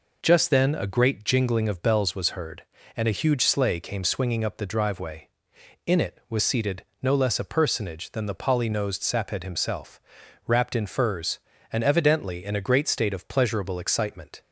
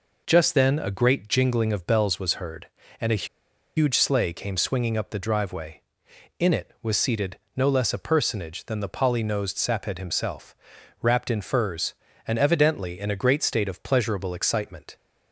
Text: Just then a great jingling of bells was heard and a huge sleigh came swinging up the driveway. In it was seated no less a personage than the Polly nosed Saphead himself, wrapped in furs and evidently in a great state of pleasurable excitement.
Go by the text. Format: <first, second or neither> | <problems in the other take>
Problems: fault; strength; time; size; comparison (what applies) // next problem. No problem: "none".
first | pauses between "a" and "huge"; noticeable; at 3.2 s; 0.51 s long // pauses between "seated" and "no"; slight; at 7.3 s; 0.18 s long; slight in the first